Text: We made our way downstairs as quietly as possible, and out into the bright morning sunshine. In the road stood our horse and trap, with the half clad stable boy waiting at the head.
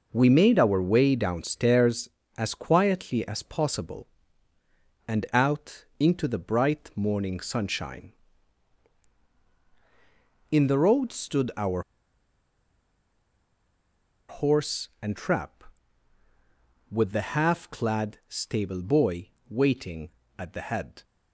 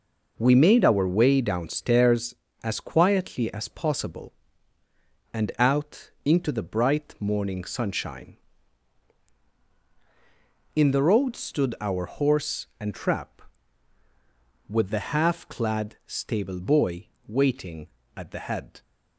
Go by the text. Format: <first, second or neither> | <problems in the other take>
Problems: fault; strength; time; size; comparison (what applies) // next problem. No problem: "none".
second | pauses between "out" and "into"; slight; at 5.8 s; 0.16 s long; slight in the second // pauses between "our" and "horse"; strong; at 11.8 s; 2.4 s long // pauses between "boy" and "waiting"; slight; at 19.3 s; 0.18 s long; slight in the second